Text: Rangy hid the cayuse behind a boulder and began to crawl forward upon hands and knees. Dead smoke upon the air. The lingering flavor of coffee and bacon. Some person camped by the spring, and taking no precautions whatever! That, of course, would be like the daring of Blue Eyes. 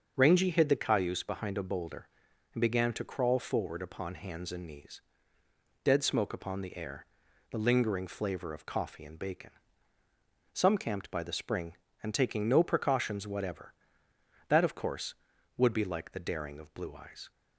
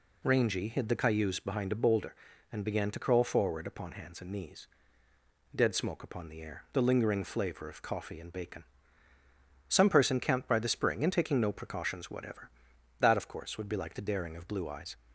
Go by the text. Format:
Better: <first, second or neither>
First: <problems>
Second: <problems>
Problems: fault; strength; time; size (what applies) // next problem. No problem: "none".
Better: second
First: starts louder than the rest; until 1.1 s; 6.5 dB // skips "person"; at 10.7 s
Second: none